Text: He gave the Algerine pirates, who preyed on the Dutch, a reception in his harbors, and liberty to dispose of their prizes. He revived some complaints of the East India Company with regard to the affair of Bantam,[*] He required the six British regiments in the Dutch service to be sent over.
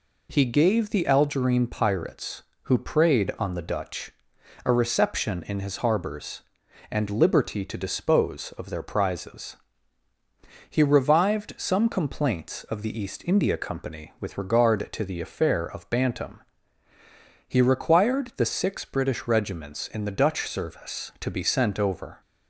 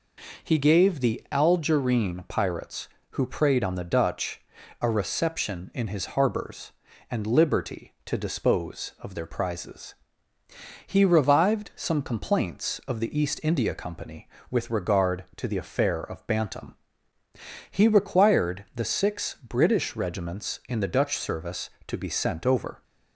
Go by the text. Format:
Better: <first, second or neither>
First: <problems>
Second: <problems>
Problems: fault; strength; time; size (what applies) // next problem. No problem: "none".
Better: neither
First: none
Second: none